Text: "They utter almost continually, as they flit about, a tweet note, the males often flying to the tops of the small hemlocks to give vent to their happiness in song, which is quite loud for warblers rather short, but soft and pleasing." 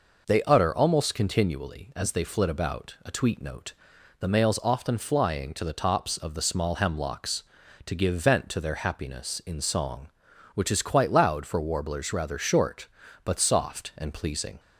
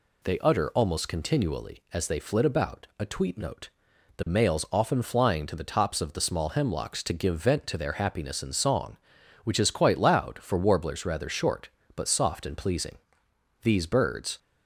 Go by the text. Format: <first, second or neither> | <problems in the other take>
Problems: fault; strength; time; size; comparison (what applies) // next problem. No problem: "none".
first | goes on to say "These birds"; noticeable; from 13.6 s on; 0.76 s long